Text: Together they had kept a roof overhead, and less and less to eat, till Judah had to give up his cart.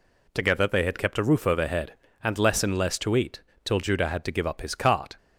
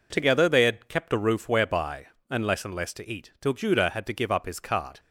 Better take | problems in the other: first | says "whereby" for "overhead"; at 1.4 s

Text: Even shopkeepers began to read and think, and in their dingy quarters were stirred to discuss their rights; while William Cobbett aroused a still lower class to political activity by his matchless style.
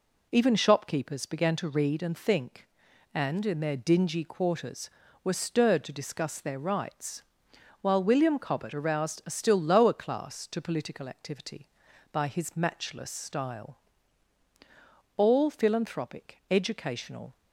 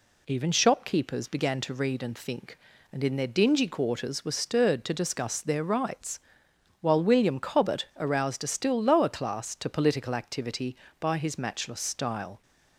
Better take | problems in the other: second | goes on to say "All philanthropic educational"; strong; from 15.1 s on; 2.1 s long

